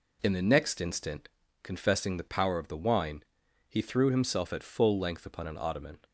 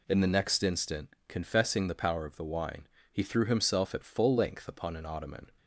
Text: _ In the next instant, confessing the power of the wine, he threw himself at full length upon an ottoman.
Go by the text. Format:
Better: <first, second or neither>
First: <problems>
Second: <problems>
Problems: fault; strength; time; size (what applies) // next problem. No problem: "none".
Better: neither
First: none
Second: none